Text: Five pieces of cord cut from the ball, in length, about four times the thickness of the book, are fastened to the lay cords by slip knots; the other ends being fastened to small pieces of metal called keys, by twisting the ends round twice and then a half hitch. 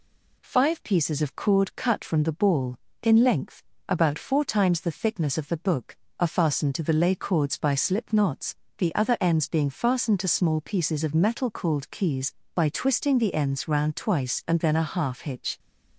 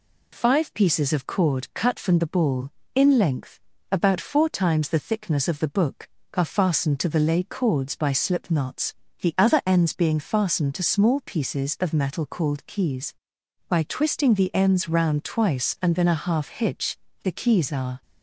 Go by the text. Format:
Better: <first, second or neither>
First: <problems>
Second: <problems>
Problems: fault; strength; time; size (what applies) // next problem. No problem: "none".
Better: first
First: none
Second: goes on to say "The keys are"; noticeable; from 17.2 s on; 0.80 s long